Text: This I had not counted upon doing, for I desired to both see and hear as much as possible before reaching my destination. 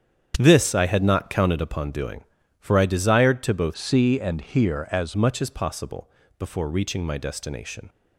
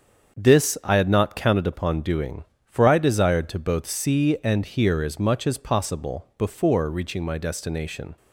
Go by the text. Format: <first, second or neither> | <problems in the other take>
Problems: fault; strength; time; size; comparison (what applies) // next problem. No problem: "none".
second | starts louder than the rest; strong; until 1.3 s; 8.5 dB; also in the second // changes voice from "see" to "as"; from 3.7 to 5.1 s; 1.4 s long // pauses between "possible" and "before"; slight; at 6.0 s; 0.30 s long